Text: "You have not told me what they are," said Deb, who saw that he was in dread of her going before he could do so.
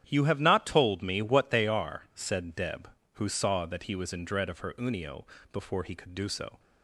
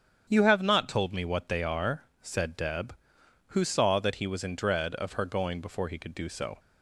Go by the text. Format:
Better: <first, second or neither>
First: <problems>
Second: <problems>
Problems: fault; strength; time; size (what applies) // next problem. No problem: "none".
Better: second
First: starts louder than the rest; strong; until 1.0 s; 10 dB // says "unio" for "going"; at 4.7 s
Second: starts louder than the rest; strong; until 1.3 s; 8 dB